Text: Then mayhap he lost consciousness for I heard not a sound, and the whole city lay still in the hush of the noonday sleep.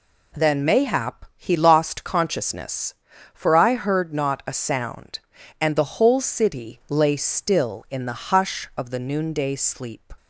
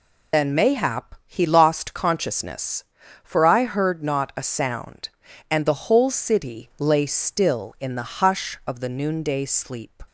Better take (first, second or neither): first